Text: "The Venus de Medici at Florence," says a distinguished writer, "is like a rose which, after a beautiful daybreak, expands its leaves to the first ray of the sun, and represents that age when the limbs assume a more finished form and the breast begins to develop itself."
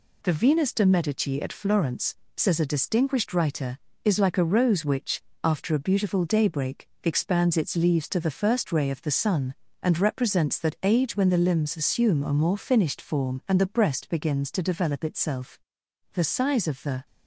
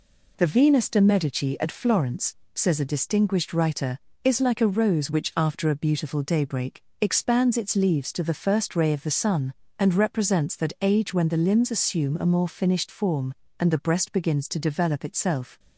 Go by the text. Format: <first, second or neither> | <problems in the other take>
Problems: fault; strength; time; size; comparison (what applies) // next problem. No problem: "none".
second | goes on to say "The size of the"; noticeable; from 16.1 s on; 0.94 s long